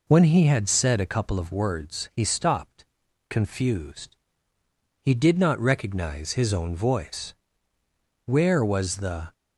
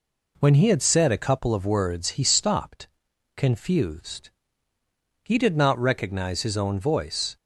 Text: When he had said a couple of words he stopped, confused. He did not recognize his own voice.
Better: second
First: goes on to say "Where was the"; noticeable; from 8.2 s on; 1.0 s long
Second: none

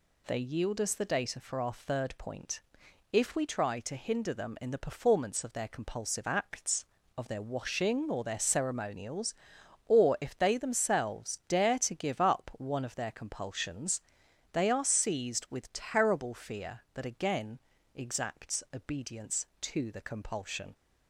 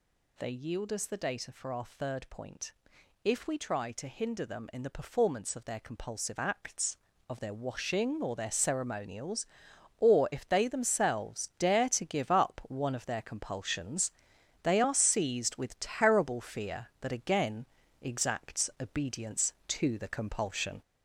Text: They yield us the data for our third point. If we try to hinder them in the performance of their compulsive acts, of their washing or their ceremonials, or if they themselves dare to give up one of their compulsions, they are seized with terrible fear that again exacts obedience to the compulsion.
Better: first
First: pauses between "again" and "exacts"; slight; at 17.6 s; 0.34 s long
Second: gets louder; throughout; 3.5 dB // pauses between "again" and "exacts"; slight; at 17.6 s; 0.34 s long

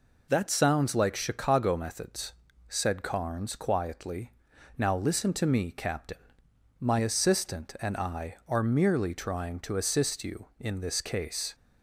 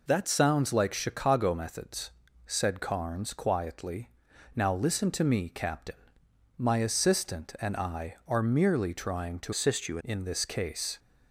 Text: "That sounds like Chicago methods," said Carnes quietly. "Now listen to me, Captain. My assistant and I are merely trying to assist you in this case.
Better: first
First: none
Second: changes voice from "assist" to "you"; from 9.5 to 9.9 s; 0.4 s long

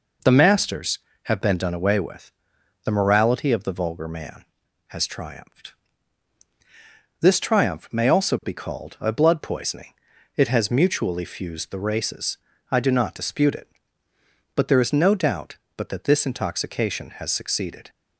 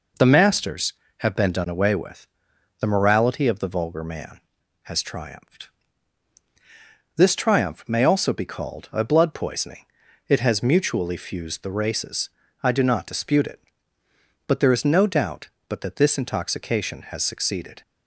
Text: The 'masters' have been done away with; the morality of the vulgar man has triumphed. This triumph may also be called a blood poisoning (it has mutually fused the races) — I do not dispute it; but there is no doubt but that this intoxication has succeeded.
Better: neither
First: none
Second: none

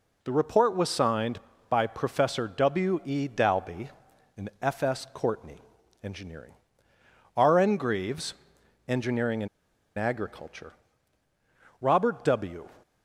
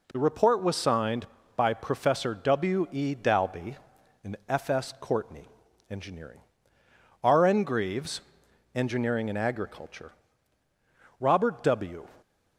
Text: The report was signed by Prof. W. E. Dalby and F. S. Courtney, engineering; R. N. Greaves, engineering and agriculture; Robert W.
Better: second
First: pauses between "and" and "agriculture"; noticeable; at 9.4 s; 0.50 s long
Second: none

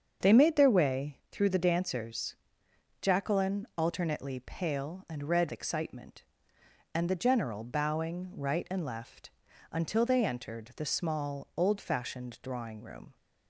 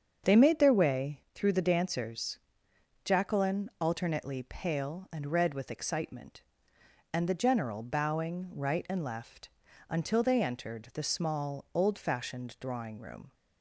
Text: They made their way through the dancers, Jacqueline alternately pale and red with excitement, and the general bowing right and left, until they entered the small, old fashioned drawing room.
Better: second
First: starts louder than the rest; until 1.3 s; 7 dB // skips "with"; at 5.5 s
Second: starts louder than the rest; until 1.3 s; 7 dB

